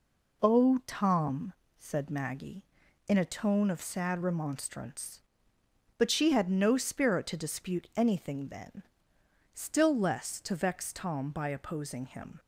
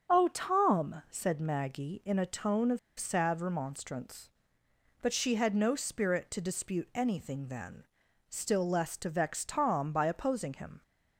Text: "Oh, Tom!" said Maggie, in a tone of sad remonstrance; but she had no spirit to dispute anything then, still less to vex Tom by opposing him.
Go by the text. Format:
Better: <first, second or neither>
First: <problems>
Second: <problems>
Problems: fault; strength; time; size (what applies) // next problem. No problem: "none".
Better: first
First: none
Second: starts louder than the rest; until 1.1 s; 7 dB // pauses between "of" and "sad"; slight; at 2.7 s; 0.20 s long